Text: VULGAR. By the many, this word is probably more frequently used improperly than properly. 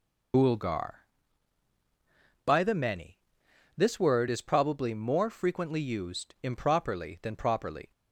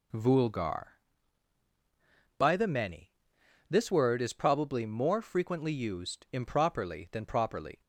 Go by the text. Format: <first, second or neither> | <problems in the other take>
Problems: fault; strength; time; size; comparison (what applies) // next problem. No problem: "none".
second | loses the start of "VULGAR"; at 0.3 s; 150 ms